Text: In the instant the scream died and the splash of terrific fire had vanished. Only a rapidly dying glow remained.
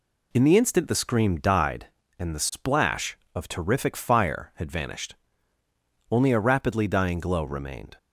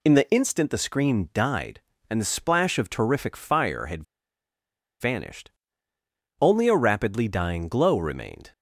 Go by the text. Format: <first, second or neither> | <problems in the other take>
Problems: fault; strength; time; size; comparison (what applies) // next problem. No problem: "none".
first | pauses between "had" and "vanished"; noticeable; at 4.0 s; 0.97 s long